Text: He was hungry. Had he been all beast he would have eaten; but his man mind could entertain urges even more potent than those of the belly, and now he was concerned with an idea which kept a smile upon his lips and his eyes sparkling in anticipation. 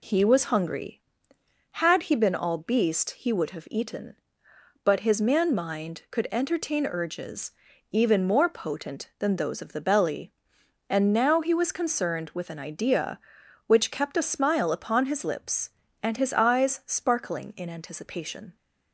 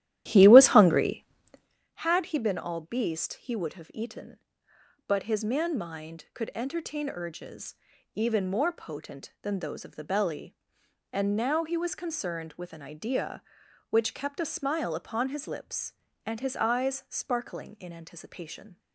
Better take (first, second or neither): first